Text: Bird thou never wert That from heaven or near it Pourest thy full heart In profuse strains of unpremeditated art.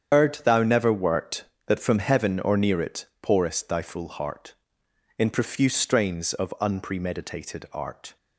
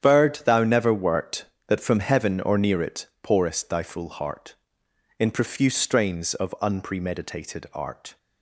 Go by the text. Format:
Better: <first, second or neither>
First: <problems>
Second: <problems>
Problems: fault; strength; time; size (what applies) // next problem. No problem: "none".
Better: second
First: loses the start of "Bird"; at 0.1 s; 95 ms // starts louder than the rest; strong; until 1.1 s; 8.5 dB // pauses between "it" and "Pourest"; slight; at 3.0 s; 0.16 s long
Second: starts louder than the rest; strong; until 1.0 s; 9.5 dB // pauses between "it" and "Pourest"; slight; at 3.0 s; 0.16 s long